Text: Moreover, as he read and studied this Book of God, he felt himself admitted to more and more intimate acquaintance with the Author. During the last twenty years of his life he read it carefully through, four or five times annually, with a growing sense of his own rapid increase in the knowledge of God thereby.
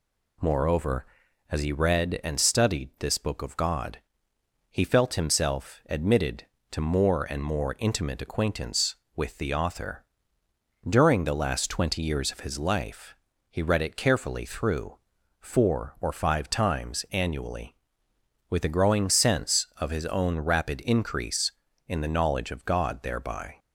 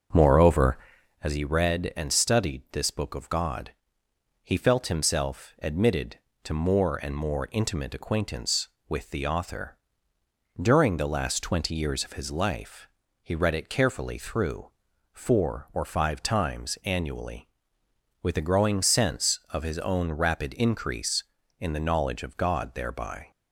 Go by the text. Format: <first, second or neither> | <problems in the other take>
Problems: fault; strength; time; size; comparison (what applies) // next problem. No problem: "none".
first | starts louder than the rest; noticeable; until 1.2 s; 5.5 dB // pauses between "life" and "he"; slight; at 12.8 s; 0.36 s long; slight in the first